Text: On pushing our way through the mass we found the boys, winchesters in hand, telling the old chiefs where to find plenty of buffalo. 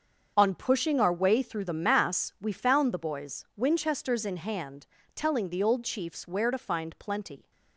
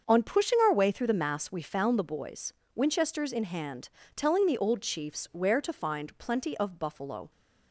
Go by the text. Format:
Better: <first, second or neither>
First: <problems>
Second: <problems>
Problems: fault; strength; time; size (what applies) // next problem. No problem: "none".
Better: second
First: starts louder than the rest; until 1.3 s; 6.5 dB // stops before "of buffalo"; at 7.5 s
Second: none